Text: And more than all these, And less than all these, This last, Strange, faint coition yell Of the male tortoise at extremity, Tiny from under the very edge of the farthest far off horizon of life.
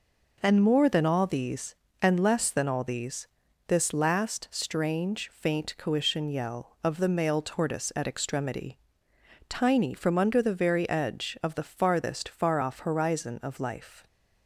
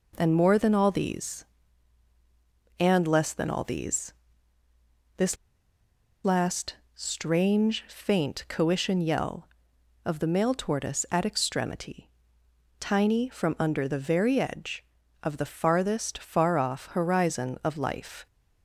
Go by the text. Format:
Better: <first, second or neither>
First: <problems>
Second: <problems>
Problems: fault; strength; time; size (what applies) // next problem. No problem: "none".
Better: first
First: none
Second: pauses between "This" and "last"; noticeable; at 5.3 s; 0.88 s long